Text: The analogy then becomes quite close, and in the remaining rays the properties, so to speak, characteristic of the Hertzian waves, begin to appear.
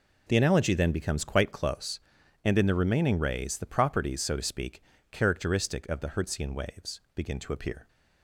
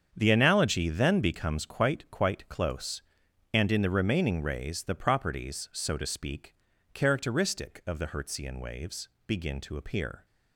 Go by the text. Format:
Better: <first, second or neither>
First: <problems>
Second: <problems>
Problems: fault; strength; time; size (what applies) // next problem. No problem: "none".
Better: first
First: none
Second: starts louder than the rest; strong; until 1.1 s; 7.5 dB // says "quite" twice; at 2.1 s